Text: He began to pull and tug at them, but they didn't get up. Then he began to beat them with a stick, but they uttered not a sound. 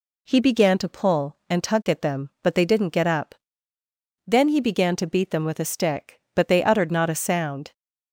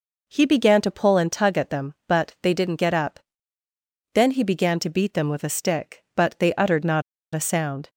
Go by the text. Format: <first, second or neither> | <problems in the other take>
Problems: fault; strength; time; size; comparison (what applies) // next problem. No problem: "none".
first | pauses between "not" and "a"; slight; at 7.0 s; 0.33 s long